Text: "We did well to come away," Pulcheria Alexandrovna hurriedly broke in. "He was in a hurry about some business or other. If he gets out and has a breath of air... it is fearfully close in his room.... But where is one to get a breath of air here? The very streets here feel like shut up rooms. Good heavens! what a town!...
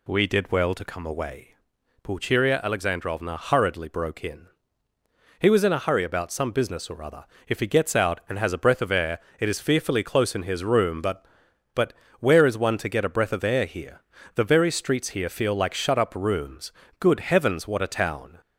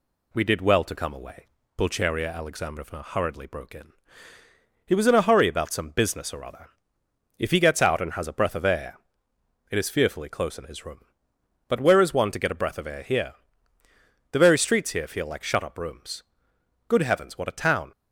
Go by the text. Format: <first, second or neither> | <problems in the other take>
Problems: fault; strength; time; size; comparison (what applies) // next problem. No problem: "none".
second | says "But" twice; at 11.7 s